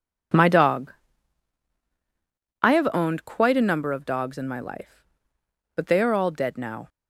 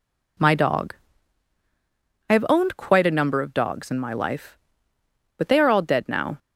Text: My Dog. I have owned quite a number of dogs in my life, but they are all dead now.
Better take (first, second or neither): neither